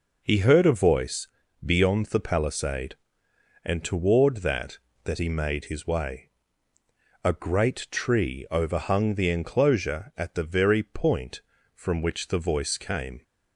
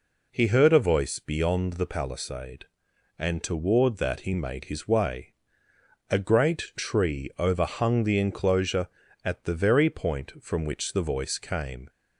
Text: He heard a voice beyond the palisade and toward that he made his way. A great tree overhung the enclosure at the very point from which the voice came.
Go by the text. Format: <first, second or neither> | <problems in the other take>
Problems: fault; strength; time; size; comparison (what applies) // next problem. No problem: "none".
second | pauses between "voice" and "beyond"; slight; at 1.2 s; 0.34 s long // says "that" twice; at 5.0 s